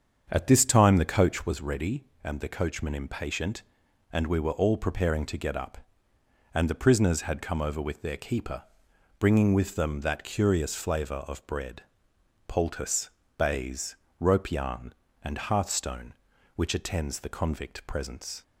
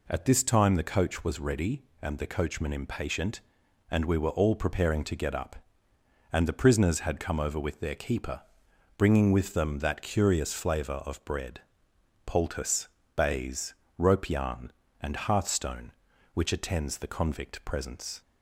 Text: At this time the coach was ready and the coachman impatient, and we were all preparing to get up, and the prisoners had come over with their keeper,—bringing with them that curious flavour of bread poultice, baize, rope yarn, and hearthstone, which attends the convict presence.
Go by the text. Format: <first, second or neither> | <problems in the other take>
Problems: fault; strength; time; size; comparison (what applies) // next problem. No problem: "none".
second | starts louder than the rest; strong; until 1.5 s; 7.5 dB // pauses between "bread" and "poultice"; noticeable; at 11.8 s; 0.64 s long; noticeable in the second